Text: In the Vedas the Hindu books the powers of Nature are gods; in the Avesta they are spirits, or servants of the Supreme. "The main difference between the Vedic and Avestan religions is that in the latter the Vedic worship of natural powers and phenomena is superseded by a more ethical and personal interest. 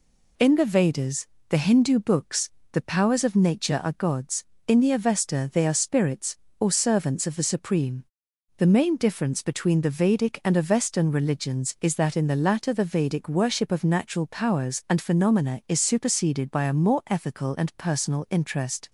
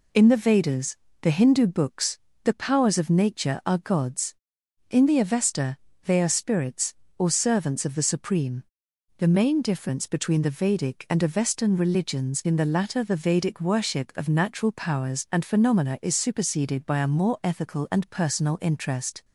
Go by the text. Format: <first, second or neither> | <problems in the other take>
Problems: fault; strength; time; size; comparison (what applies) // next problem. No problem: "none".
first | pauses between "Vedas" and "the"; slight; at 0.9 s; 0.26 s long; slight in the first // pauses between "books" and "the"; slight; at 2.1 s; 0.24 s long; slight in the first // pauses between "Avesta" and "they"; slight; at 5.7 s; 0.28 s long // skips "is that"; at 12.4 s